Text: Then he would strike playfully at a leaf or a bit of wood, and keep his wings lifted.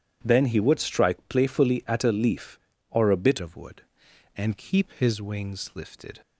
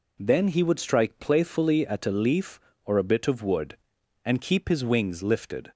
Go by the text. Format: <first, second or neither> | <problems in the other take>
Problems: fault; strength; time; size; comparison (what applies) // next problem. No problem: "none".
second | starts louder than the rest; strong; until 1.2 s; 10 dB // changes voice at "of"; from 3.4 s on; 2.8 s long